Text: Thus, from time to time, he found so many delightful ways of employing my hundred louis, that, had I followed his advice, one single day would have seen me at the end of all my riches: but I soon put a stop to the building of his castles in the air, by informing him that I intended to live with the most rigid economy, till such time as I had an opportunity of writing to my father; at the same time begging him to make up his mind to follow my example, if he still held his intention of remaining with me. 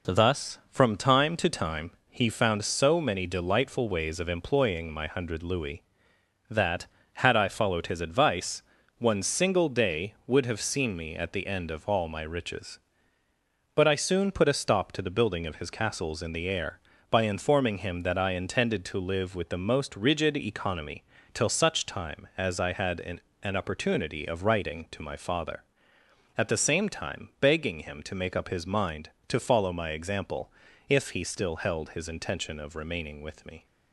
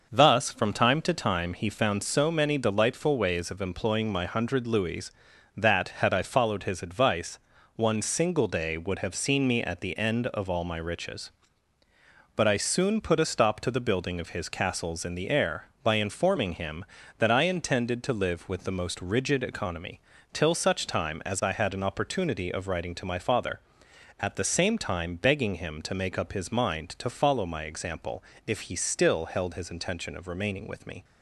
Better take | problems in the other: second | says "an" twice; at 23.4 s

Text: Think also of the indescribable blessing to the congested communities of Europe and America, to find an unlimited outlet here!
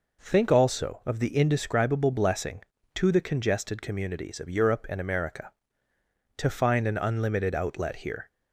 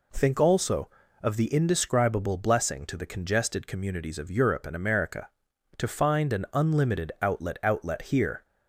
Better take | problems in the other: first | says "outlet" twice; at 7.6 s

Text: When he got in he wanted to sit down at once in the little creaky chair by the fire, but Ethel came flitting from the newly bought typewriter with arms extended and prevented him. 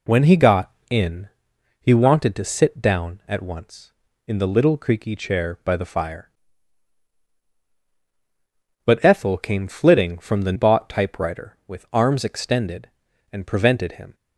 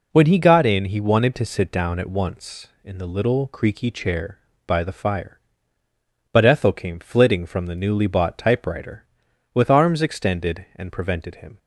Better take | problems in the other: second | pauses between "in" and "he"; noticeable; at 1.2 s; 0.54 s long // skips "newly"; at 10.5 s

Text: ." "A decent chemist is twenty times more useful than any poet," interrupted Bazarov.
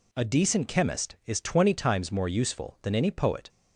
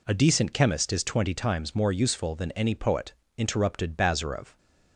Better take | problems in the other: second | stops before "interrupted Bazarov"; at 3.4 s

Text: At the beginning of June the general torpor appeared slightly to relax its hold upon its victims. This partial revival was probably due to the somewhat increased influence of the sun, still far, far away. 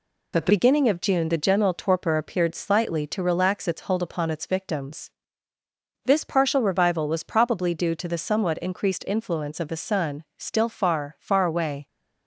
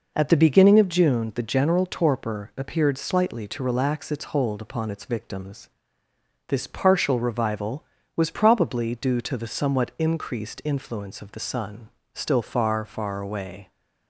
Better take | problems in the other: second | changes voice at "beginning"; from 0.4 s on; 11.4 s long

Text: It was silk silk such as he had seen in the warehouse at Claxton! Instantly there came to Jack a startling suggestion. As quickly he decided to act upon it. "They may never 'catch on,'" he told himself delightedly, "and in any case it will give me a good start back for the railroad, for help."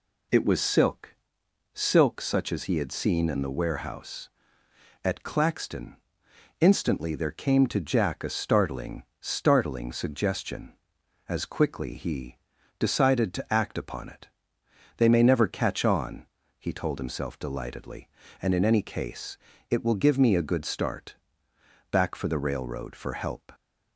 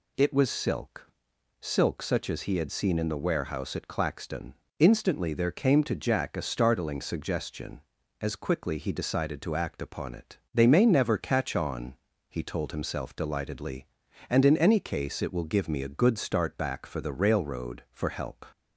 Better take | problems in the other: second | pauses between "silk" and "silk"; noticeable; at 1.1 s; 0.58 s long; noticeable in the second // says "startling" twice; at 9.1 s // pauses between "he" and "decided"; at 12.3 s; 0.40 s long // pauses between "case" and "it"; slight; at 19.3 s; 0.36 s long // pauses between "start" and "back"; noticeable; at 21.1 s; 0.74 s long

